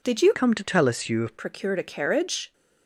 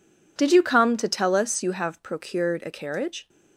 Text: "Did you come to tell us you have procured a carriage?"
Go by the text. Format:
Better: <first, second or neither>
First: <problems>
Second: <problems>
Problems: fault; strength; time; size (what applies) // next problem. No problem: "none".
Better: second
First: changes voice from "come" to "have"; from 0.3 to 1.3 s; 1.0 s long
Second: none